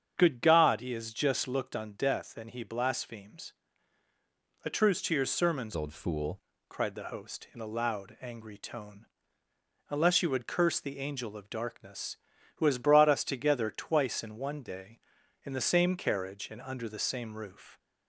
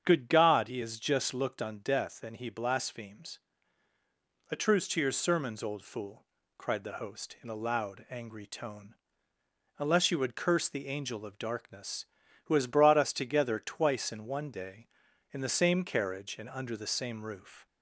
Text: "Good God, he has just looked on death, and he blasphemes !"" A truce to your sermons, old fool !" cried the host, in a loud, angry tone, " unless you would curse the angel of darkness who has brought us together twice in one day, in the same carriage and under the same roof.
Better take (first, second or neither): second